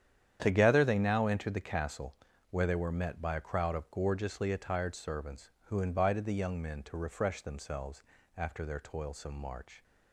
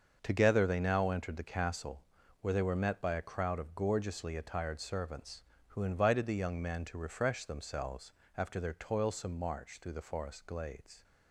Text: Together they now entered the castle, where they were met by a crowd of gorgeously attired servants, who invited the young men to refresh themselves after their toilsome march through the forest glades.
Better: second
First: starts louder than the rest; strong; until 1.4 s; 9.5 dB // pauses between "themselves" and "after"; slight; at 8.0 s; 0.34 s long // stops before "through the forest glades"; at 9.8 s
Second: starts louder than the rest; until 1.2 s; 6.5 dB // pauses between "themselves" and "after"; slight; at 8.1 s; 0.26 s long

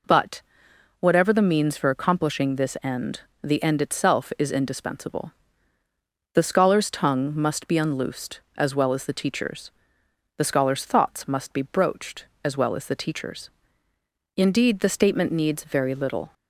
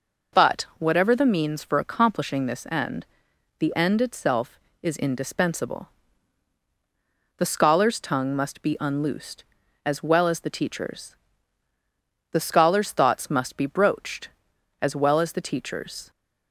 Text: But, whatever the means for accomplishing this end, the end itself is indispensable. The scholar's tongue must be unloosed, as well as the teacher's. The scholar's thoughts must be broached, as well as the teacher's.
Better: second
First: goes on to say "Indeed the statement needs very little"; strong; from 14.3 s on; 1.9 s long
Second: none

